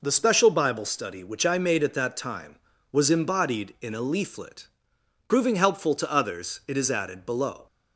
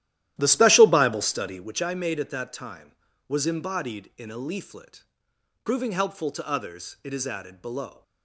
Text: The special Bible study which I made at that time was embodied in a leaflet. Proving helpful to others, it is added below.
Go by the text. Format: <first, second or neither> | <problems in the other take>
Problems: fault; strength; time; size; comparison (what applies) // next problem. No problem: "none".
first | starts louder than the rest; strong; until 1.8 s; 13 dB